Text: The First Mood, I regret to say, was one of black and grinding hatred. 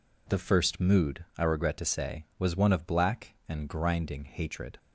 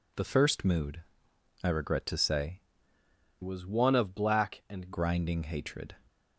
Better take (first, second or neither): first